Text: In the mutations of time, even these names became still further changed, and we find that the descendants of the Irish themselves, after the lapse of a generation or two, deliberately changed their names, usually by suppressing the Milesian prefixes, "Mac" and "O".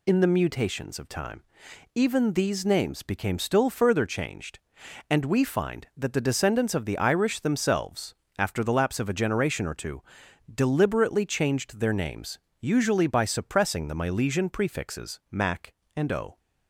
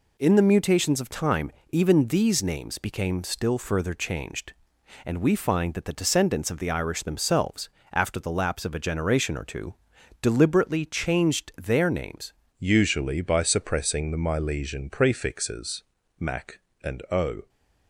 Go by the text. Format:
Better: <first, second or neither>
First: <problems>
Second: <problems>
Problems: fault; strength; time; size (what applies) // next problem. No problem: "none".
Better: first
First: none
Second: changes voice at "usually"; from 12.5 s on; 4.9 s long